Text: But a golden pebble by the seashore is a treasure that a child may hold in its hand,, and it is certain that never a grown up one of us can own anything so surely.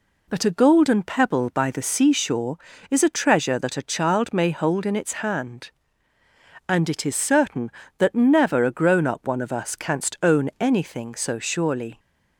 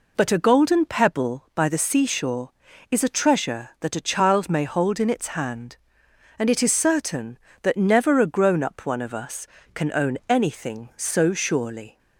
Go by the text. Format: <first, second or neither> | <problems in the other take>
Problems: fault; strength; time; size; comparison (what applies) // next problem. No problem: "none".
second | says "canst" for "can"; at 9.7 s